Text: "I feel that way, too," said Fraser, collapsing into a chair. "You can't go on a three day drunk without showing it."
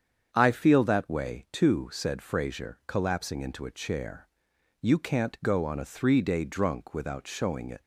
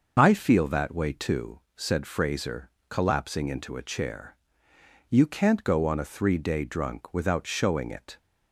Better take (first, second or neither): neither